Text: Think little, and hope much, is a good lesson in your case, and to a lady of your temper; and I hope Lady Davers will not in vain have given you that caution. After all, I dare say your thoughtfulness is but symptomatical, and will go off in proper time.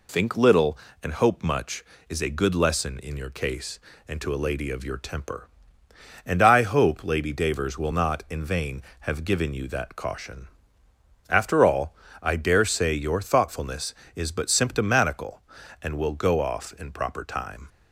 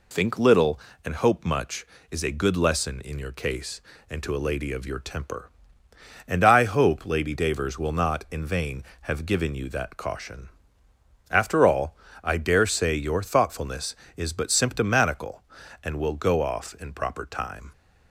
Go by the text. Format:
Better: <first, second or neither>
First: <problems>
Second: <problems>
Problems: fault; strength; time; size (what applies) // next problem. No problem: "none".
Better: neither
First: none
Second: none